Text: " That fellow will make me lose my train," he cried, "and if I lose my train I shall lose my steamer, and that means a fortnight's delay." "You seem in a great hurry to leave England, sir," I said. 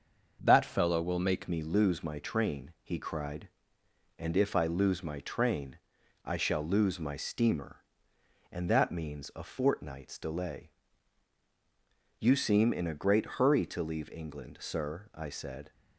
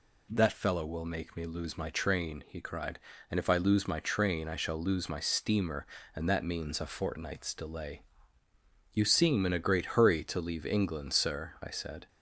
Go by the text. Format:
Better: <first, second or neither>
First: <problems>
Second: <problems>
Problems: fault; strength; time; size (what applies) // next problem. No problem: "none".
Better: second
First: starts louder than the rest; until 1.4 s; 6.5 dB // changes voice at "me"; from 1.4 s on; 14.3 s long // pauses between "train" and "I"; noticeable; at 5.7 s; 0.48 s long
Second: none